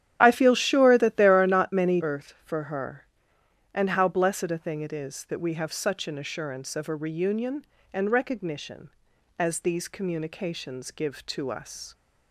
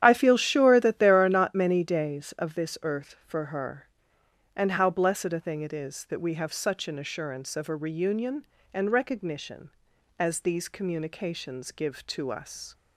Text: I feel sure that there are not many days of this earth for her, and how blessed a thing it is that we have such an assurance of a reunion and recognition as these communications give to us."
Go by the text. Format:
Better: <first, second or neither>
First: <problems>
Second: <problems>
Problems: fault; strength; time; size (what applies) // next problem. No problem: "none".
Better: second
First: starts louder than the rest; strong; until 1.2 s; 10.5 dB // skips "days of this"; at 1.9 s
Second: starts louder than the rest; strong; until 1.0 s; 10 dB